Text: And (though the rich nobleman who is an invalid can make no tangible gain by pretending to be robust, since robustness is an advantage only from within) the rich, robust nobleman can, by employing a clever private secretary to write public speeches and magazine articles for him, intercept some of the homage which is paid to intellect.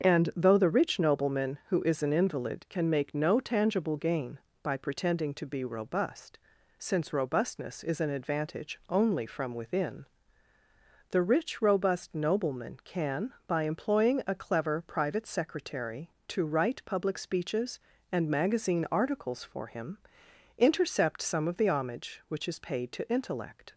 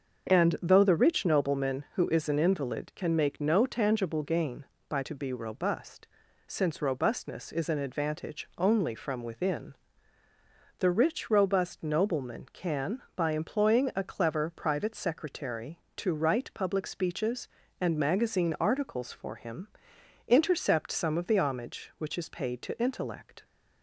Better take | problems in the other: first | starts louder than the rest; until 1.3 s; 6.5 dB; also in the first // skips "pretending"; at 5.0 s

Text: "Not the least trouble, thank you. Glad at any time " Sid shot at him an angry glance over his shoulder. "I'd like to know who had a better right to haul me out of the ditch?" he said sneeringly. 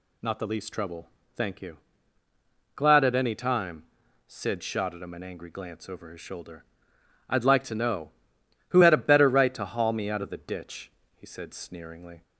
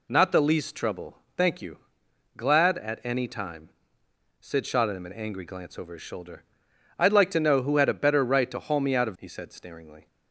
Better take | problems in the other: first | skips "the ditch"; at 9.1 s

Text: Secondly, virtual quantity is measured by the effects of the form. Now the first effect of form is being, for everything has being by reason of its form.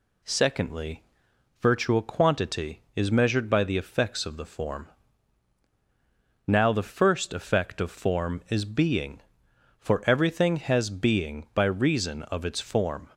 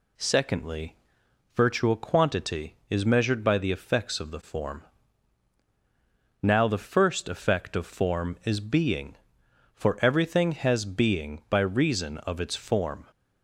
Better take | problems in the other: neither | none

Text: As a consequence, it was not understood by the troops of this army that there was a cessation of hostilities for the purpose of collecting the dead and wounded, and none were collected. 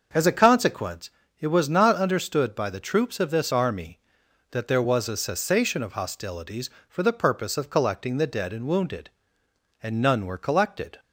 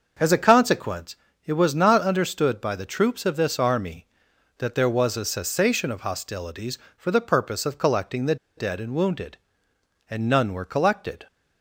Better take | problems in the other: first | starts louder than the rest; until 1.5 s; 6.5 dB; also in the first // pauses between "the" and "dead"; slight; at 8.3 s; 0.21 s long

